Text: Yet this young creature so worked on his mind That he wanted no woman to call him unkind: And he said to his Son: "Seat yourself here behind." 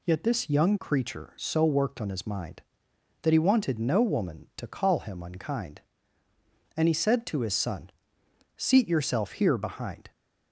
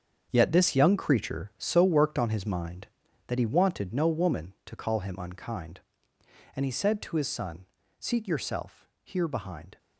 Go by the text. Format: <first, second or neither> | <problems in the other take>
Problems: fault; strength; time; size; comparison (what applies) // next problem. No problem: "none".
first | gets quieter; strong; throughout; 11 dB // pauses between "yourself" and "here"; slight; at 8.8 s; 0.16 s long